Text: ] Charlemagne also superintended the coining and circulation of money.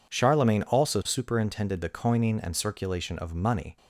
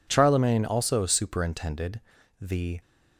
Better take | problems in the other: first | pauses between "superintended" and "the"; at 1.9 s; 0.41 s long // stops before "coining and circulation of money"; at 2.8 s

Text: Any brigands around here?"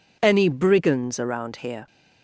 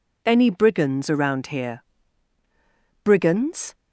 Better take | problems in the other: first | goes on to say "Brigands"; noticeable; from 3.0 s on; 0.70 s long

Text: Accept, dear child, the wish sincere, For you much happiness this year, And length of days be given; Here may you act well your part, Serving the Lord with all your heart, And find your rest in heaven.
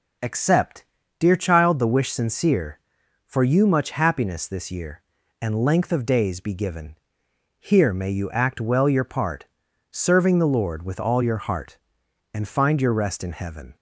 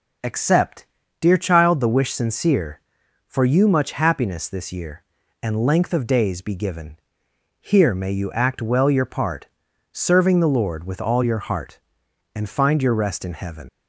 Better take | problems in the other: first | leaves "heaven" unfinished; at 13.6 s; 80 ms

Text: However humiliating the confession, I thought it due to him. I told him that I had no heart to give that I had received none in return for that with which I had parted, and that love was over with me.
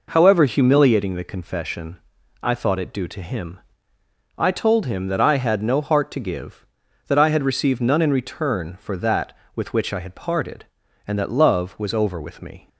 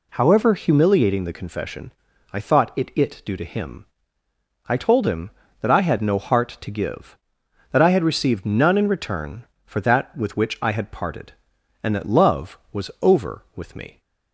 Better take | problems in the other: first | says "it" twice; at 2.9 s

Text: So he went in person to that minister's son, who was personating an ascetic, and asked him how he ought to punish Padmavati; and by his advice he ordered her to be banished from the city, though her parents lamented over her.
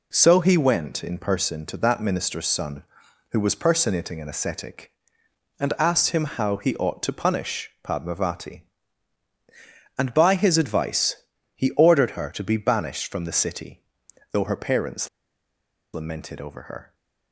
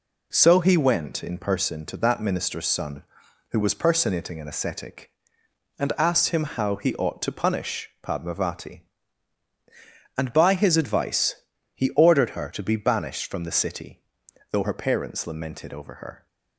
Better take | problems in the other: second | pauses between "advice" and "he"; at 11.1 s; 0.40 s long; also in the second // pauses between "parents" and "lamented"; noticeable; at 15.0 s; 0.85 s long

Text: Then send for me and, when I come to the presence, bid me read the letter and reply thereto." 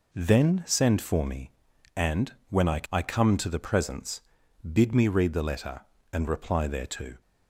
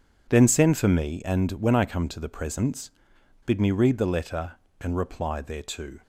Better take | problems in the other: second | says "I" twice; at 2.9 s

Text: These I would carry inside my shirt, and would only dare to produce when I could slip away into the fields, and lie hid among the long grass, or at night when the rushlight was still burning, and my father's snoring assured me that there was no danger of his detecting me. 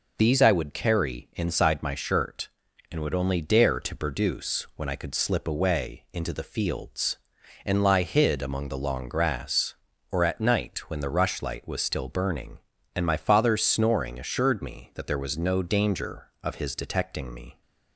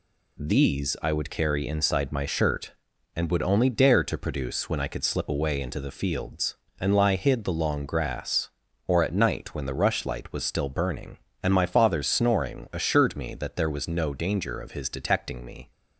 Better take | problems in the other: first | skips "among"; at 7.4 s

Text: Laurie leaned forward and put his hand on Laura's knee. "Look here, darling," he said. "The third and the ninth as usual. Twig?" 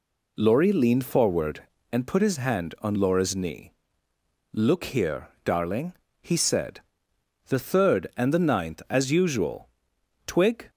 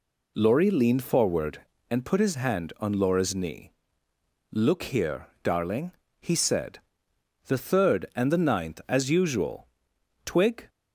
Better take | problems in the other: neither | none

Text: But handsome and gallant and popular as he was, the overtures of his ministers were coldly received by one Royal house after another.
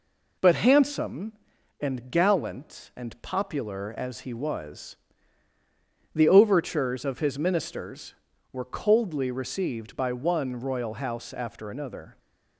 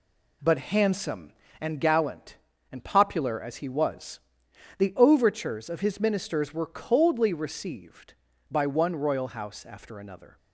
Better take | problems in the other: neither | none

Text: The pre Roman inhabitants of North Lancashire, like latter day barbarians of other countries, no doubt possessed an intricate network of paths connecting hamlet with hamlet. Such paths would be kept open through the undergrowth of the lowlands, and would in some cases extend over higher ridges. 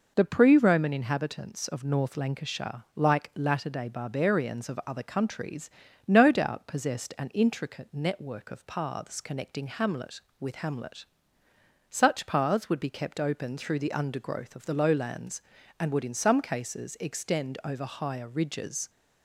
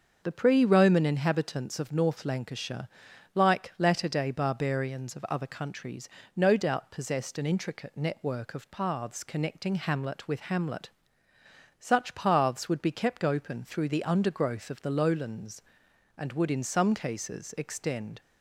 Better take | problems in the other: first | starts louder than the rest; until 1.2 s; 6.5 dB // stops before "over higher ridges"; at 18.2 s

